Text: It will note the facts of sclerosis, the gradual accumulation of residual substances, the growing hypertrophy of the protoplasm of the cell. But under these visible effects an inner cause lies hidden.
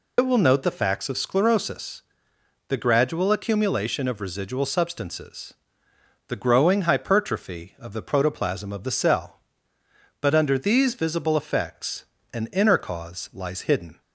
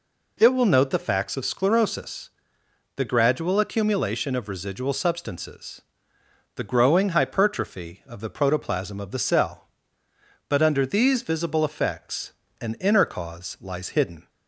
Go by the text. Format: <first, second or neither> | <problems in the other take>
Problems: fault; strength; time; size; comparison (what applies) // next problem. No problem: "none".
second | loses the start of "It"; at 0.1 s; 75 ms // pauses between "effects" and "an"; slight; at 12.0 s; 0.28 s long; slight in the second